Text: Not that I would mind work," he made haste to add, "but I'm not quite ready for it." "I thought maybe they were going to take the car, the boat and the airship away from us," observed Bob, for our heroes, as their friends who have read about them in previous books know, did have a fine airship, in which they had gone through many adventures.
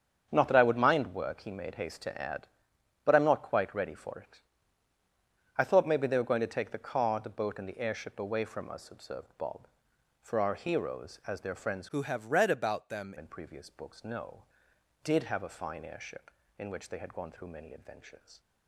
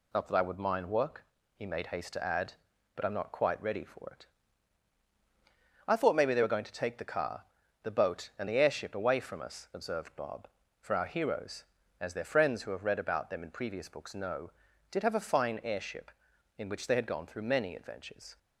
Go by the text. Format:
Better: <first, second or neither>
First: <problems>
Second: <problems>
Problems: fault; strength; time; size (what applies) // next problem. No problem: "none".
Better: second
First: starts louder than the rest; strong; until 1.3 s; 7.5 dB // changes voice from "who" to "them"; from 11.8 to 13.1 s; 1.3 s long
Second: none